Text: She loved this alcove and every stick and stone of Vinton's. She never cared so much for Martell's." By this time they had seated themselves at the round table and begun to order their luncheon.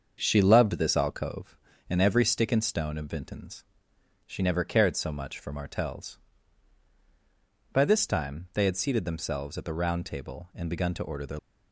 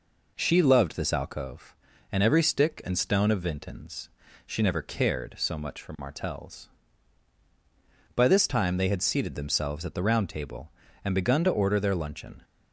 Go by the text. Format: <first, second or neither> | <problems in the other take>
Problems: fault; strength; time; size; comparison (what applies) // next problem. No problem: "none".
second | starts louder than the rest; until 1.2 s; 6.5 dB // stops before "luncheon"; at 11.3 s